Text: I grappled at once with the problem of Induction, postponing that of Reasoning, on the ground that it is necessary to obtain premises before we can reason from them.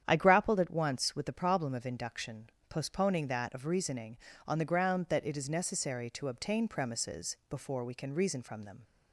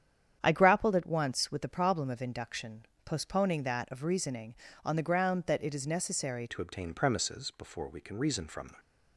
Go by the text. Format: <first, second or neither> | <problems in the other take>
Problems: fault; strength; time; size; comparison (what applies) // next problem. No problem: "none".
first | starts louder than the rest; strong; until 1.4 s; 9 dB; strong in the first // changes voice at "to"; from 6.4 s on; 2.3 s long